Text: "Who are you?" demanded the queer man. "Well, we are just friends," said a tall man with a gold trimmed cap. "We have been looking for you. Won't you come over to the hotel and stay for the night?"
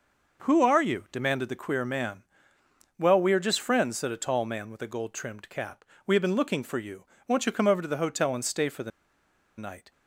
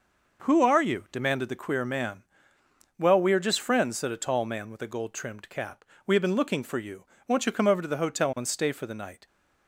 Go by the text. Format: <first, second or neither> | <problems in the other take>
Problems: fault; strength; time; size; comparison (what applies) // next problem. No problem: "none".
second | pauses between "the" and "night"; noticeable; at 8.9 s; 0.67 s long